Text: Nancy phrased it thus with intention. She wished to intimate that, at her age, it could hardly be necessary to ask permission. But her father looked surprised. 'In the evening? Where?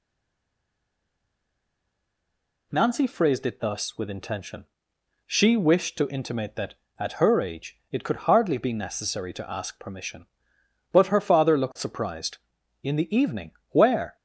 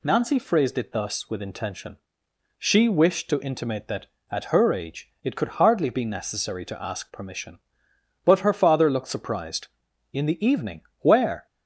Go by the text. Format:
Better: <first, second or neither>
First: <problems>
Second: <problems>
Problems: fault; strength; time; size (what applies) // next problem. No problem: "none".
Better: second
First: stays silent before the first word; strong; until 2.7 s; 2.7 s long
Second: none